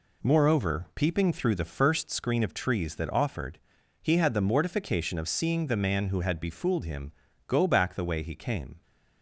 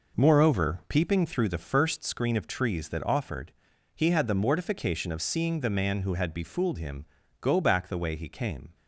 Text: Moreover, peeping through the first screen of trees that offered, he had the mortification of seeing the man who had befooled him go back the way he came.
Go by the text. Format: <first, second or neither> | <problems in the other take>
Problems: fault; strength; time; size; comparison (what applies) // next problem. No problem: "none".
first | starts louder than the rest; noticeable; until 1.3 s; 5 dB // pauses between "him" and "go"; slight; at 7.0 s; 0.36 s long; slight in the first